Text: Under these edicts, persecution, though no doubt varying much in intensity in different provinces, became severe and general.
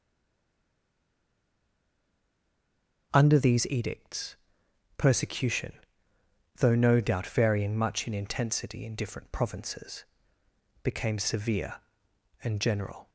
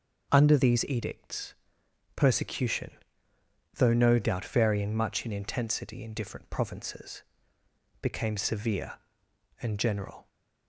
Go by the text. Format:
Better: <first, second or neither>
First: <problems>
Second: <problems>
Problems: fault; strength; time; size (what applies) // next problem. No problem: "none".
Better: second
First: stays silent before the first word; strong; until 3.1 s; 3.1 s long // starts louder than the rest; until 4.1 s; 6.5 dB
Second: starts louder than the rest; until 1.3 s; 6.5 dB